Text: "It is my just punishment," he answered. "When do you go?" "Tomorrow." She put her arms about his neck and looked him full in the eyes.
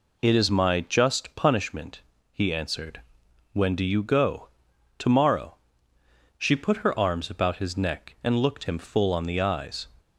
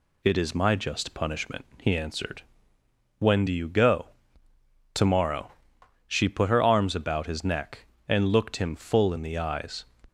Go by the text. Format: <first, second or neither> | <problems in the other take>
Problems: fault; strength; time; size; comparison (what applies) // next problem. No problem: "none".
second | says "on" for "in"; at 9.1 s